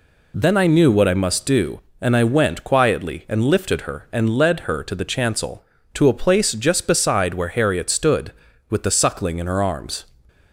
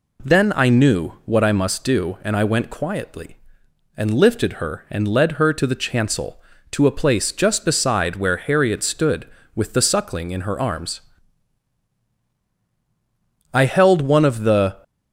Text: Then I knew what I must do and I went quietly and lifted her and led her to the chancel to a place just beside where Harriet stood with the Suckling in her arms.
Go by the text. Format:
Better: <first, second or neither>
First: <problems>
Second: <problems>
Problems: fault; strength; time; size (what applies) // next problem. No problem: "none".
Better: first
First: none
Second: goes on to say "I held one of the"; noticeable; from 13.5 s on; 1.2 s long